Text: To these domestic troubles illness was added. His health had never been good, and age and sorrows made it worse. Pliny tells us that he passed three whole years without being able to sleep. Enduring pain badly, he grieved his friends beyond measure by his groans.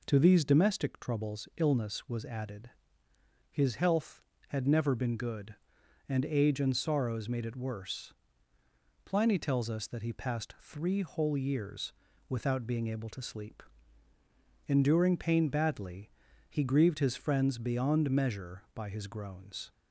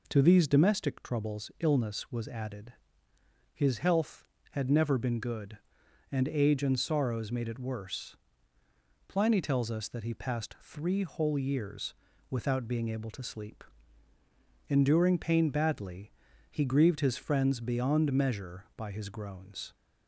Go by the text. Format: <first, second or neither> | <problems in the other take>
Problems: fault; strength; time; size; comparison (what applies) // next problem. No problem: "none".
neither | pauses between "years" and "without"; slight; the same in both